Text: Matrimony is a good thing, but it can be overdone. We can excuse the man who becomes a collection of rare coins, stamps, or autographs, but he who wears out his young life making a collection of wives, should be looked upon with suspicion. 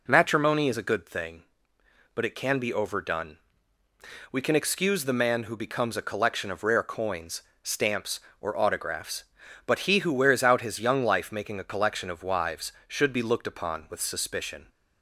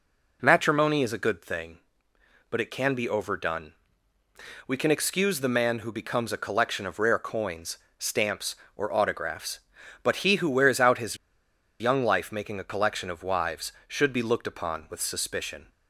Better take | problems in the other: first | pauses between "his" and "young"; noticeable; at 11.1 s; 0.64 s long

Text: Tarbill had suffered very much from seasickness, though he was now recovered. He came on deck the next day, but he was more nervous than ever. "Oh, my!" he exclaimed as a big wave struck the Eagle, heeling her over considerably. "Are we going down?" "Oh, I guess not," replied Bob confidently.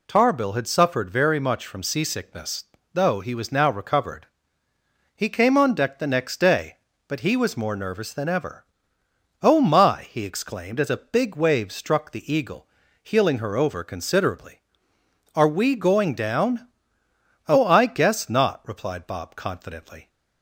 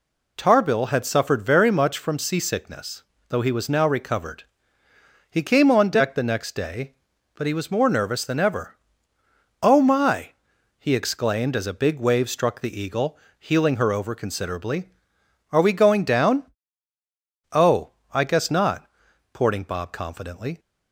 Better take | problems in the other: first | says "porting" for "replied"; at 19.3 s

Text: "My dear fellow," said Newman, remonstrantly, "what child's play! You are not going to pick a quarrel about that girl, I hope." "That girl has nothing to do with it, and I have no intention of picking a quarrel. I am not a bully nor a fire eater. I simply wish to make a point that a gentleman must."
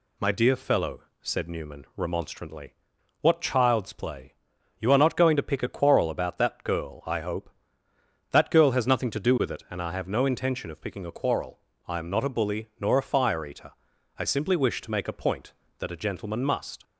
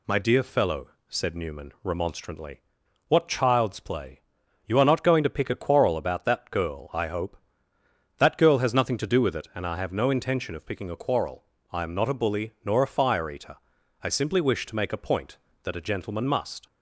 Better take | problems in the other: neither | none

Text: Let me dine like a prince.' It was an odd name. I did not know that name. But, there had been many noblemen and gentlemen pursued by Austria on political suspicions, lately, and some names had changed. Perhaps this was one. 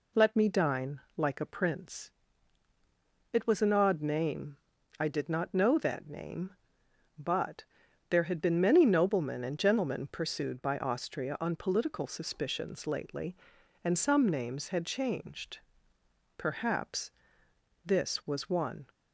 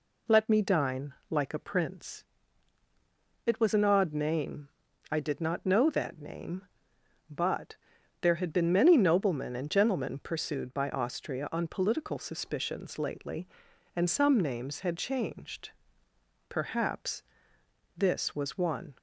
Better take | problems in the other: neither | pauses between "dine" and "like"; slight; the same in both // pauses between "Perhaps" and "this"; noticeable; the same in both

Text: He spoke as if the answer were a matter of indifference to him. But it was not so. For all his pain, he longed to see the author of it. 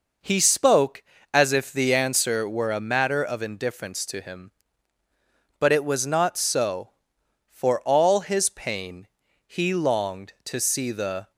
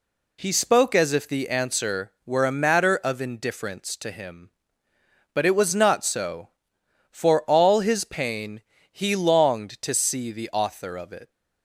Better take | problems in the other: second | stops before "author of it"; at 11.3 s

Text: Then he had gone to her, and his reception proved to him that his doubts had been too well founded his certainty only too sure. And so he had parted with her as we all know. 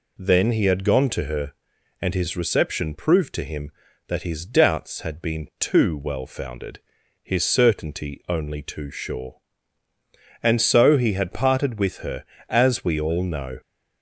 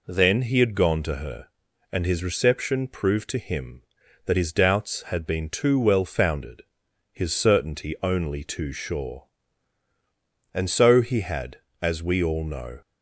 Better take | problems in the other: first | pauses between "founded" and "his"; noticeable; at 6.6 s; 0.52 s long; noticeable in the first // skips "parted with her"; at 11.6 s

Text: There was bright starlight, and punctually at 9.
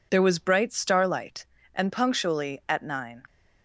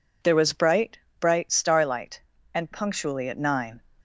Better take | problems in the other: first | says "bright" twice; at 1.1 s

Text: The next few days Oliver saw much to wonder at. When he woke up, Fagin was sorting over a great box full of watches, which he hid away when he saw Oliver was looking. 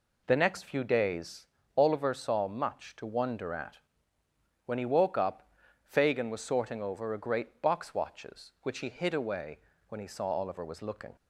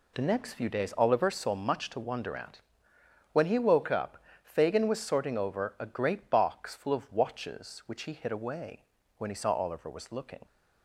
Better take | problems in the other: second | pauses between "days" and "Oliver"; slight; at 1.4 s; 0.29 s long // skips "full of"; at 7.9 s // pauses between "away" and "when"; slight; at 9.5 s; 0.30 s long; slight in the second

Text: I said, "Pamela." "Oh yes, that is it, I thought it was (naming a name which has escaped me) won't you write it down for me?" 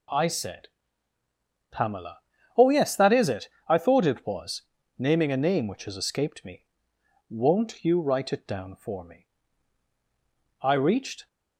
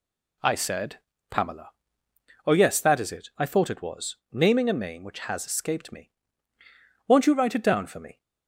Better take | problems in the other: second | goes on to say "I reached"; noticeable; from 10.6 s on; 0.64 s long

